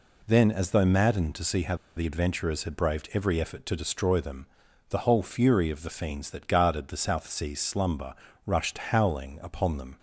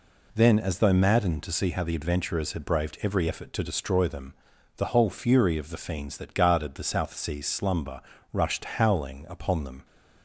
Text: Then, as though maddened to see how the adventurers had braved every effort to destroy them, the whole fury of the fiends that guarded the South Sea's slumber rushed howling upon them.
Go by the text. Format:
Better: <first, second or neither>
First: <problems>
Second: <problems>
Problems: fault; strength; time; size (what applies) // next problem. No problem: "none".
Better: second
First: pauses between "how" and "the"; slight; at 1.7 s; 0.21 s long // pauses between "slumber" and "rushed"; slight; at 8.1 s; 0.30 s long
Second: pauses between "slumber" and "rushed"; slight; at 8.0 s; 0.30 s long